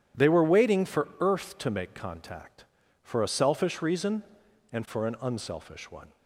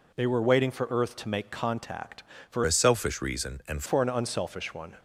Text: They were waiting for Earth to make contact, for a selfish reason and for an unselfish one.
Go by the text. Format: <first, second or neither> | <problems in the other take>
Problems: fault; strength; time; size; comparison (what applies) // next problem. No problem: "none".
first | changes voice from "a" to "and"; from 2.6 to 3.8 s; 1.2 s long